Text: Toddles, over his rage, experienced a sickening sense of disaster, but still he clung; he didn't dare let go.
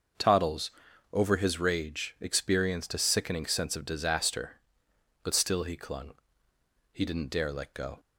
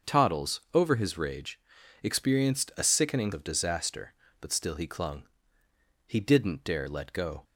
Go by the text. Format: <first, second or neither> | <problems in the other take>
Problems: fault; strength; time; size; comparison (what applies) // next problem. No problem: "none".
first | starts louder than the rest; until 1.2 s; 6 dB; noticeable in the first // skips "sense"; at 3.3 s